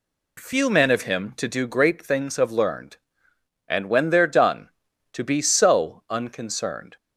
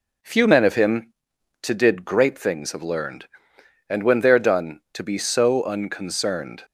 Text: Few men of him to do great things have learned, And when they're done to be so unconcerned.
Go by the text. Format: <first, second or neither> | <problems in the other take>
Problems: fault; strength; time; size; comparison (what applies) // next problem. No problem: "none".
first | says "did" for "do"; at 1.7 s